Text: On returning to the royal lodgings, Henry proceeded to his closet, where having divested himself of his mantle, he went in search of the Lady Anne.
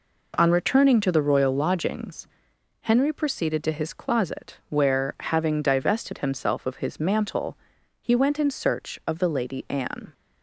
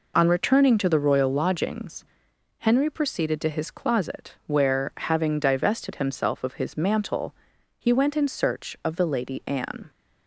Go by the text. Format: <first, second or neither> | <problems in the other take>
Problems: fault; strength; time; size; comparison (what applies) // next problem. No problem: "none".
first | loses the start of "On"; at 0.1 s; 30 ms